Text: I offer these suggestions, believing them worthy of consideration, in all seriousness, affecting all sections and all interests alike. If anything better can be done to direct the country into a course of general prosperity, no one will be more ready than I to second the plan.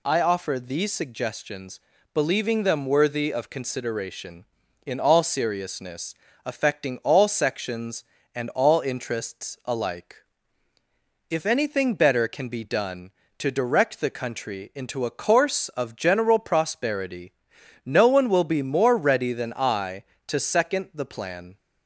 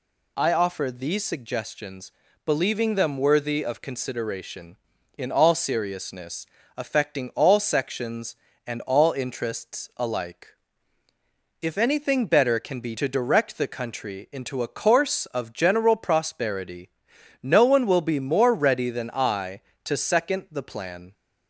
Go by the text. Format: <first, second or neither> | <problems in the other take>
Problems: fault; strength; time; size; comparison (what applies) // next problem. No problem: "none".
first | skips "done"; at 12.9 s